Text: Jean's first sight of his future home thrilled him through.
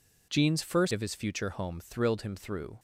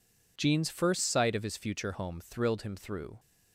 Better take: second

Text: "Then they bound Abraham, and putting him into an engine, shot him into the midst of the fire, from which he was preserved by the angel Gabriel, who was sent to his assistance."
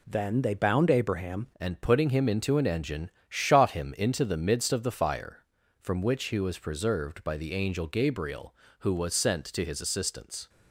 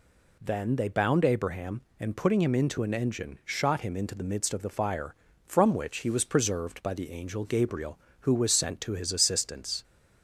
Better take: second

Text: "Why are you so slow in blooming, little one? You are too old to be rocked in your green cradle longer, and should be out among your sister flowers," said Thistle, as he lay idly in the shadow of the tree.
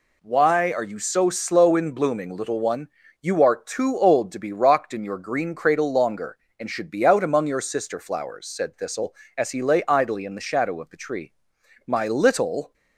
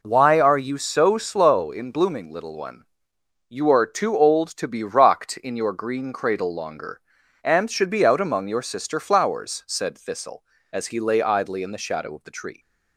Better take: second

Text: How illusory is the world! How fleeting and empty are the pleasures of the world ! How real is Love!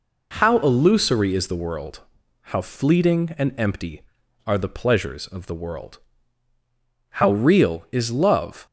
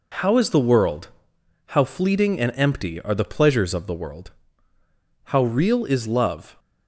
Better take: first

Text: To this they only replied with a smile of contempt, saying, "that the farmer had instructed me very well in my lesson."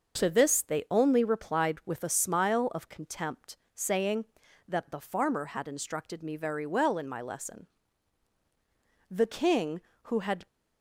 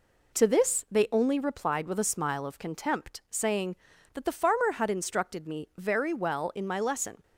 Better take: second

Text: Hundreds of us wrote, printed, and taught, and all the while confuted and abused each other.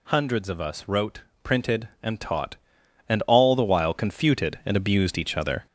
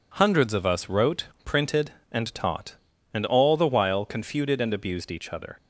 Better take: second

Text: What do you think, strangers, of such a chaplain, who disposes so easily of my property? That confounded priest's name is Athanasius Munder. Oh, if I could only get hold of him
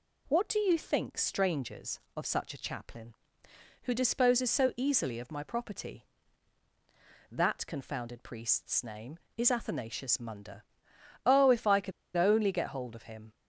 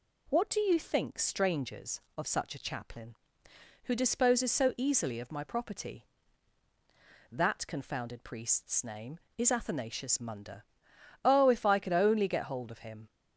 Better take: second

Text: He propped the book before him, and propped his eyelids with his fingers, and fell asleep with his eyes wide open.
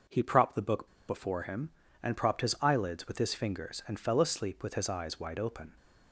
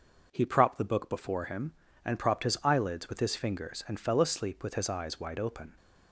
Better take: second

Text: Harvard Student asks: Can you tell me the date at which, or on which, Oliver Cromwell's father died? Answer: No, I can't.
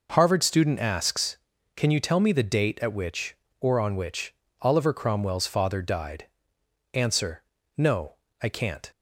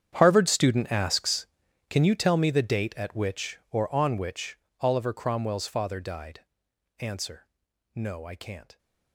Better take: first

